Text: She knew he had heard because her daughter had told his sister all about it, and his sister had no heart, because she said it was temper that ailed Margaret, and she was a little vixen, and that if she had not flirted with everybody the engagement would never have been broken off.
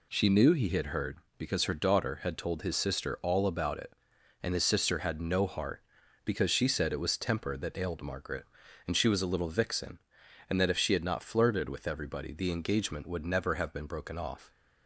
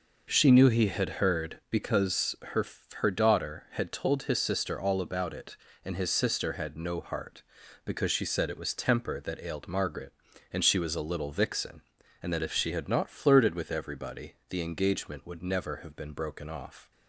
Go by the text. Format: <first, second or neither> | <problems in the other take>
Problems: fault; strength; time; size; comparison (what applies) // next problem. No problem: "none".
first | says "her" twice; at 2.9 s // pauses between "everybody" and "the"; slight; at 14.3 s; 0.16 s long